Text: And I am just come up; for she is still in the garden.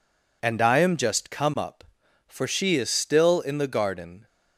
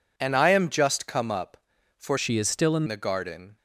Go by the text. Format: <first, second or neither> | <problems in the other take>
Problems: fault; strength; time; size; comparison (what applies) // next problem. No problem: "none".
first | changes voice from "she" to "in"; from 2.1 to 2.8 s; 0.7 s long